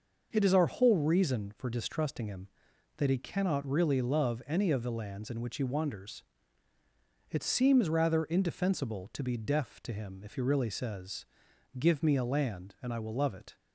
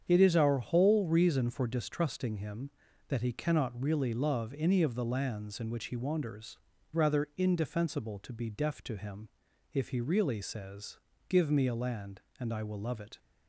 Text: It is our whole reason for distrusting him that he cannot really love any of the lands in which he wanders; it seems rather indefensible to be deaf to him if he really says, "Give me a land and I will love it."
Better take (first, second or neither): first